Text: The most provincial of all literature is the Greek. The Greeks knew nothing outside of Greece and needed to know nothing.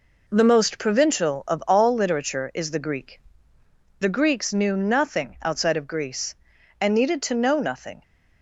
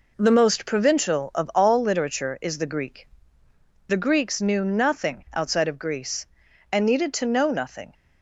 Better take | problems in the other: neither | none

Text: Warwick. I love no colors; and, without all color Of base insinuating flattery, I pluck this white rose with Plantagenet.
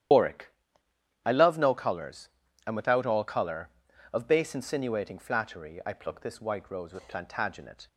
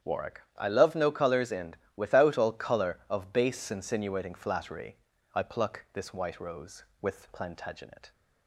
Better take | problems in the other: second | loses the start of "Warwick"; at 0.1 s; 80 ms // starts louder than the rest; strong; until 1.8 s; 11 dB; strong in the second

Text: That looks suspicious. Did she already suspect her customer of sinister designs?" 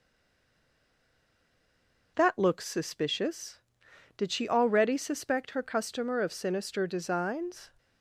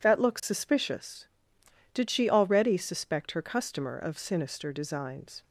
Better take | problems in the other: second | stays silent before the first word; until 2.1 s; 2.1 s long

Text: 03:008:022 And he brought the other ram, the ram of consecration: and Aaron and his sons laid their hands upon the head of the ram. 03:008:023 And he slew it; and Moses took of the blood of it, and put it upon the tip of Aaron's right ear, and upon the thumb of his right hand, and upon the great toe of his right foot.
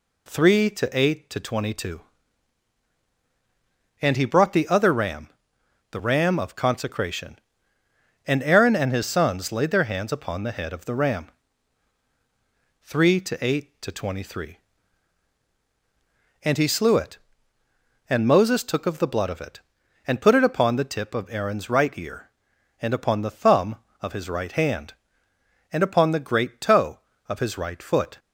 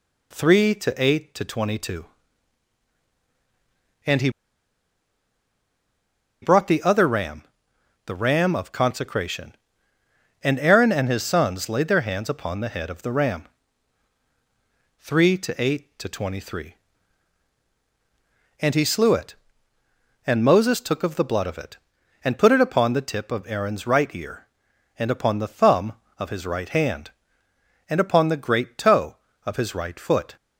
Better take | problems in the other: first | pauses between "he" and "brought"; strong; at 4.2 s; 2.1 s long

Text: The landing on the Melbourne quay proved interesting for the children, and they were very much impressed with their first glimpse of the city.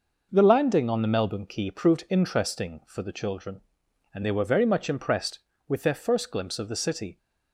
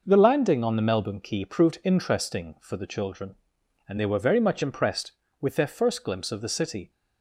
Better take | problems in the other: neither | none

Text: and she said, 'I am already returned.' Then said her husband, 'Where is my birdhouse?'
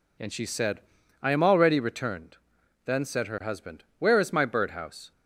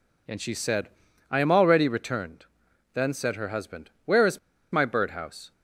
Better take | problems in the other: first | pauses between "is" and "my"; slight; at 4.3 s; 0.34 s long

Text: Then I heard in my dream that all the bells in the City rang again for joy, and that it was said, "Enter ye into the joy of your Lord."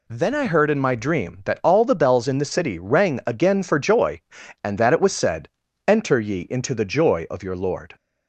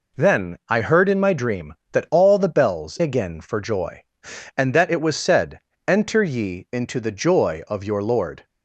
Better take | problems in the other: first | skips "in the City rang"; at 2.9 s

